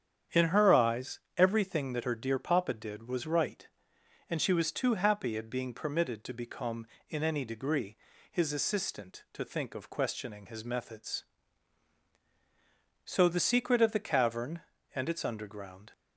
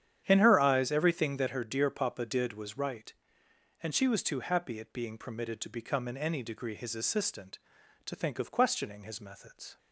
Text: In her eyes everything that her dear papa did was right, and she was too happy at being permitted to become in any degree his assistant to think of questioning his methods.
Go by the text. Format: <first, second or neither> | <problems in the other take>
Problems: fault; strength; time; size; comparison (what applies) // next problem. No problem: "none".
second | starts louder than the rest; strong; until 1.4 s; 8.5 dB; strong in the second // pauses between "eyes" and "everything"; slight; at 1.1 s; 0.18 s long // pauses between "degree" and "his"; slight; at 7.9 s; 0.34 s long // goes on to say "So the secret of the cavern and its underground"; strong; from 13.0 s on; 2.8 s long